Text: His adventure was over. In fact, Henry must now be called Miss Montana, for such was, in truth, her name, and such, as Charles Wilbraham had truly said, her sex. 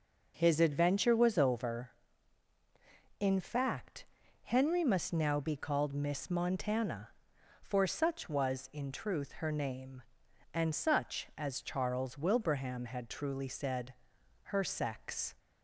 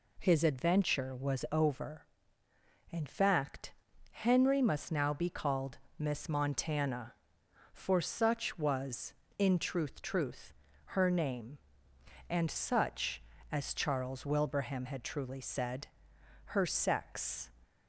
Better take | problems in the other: first | pauses between "called" and "Miss"; slight; at 5.7 s; 0.20 s long // says "truth" twice; at 10.0 s

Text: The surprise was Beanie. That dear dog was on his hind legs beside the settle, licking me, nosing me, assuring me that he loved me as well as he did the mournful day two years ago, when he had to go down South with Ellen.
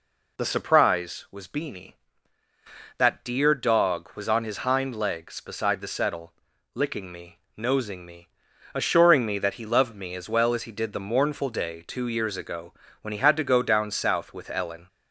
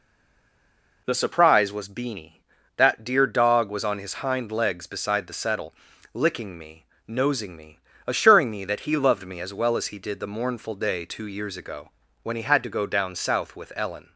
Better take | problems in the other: first | stays silent before the first word; until 1.0 s; 1.0 s long

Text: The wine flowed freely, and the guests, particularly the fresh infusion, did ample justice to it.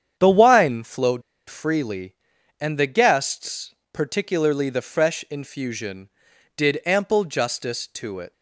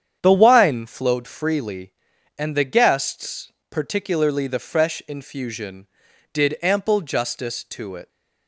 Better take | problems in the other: second | starts louder than the rest; strong; until 1.2 s; 8.5 dB; strong in the second // pauses between "flowed" and "freely"; slight; at 1.2 s; 0.26 s long

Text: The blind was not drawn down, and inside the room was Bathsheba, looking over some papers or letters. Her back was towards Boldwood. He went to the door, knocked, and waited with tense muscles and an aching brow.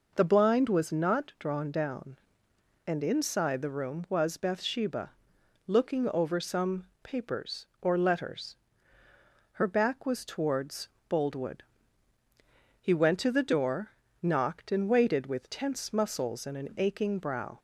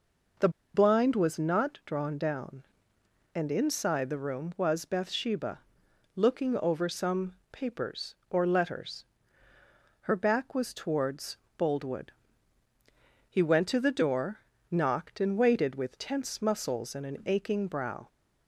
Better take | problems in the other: first | pauses between "The" and "blind"; slight; at 0.4 s; 0.25 s long // pauses between "some" and "papers"; slight; at 7.3 s; 0.16 s long; slight in the first // pauses between "towards" and "Boldwood"; slight; at 11.3 s; 0.22 s long; slight in the first

